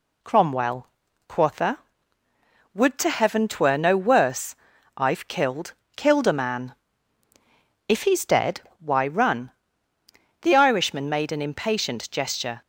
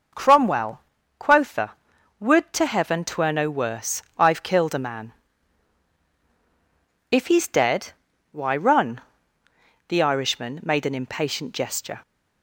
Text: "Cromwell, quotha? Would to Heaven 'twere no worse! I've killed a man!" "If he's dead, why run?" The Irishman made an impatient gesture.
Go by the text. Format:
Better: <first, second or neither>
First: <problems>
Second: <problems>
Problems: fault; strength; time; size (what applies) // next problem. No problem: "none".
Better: second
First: says "killed" twice; at 5.9 s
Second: none